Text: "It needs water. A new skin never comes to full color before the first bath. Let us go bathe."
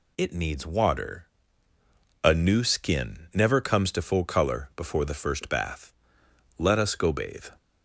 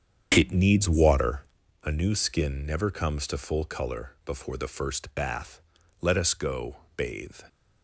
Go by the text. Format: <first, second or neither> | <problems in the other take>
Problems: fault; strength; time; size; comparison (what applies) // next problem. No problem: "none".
first | starts louder than the rest; strong; until 1.6 s; 7.5 dB // pauses between "go" and "bathe"; slight; at 6.7 s; 0.20 s long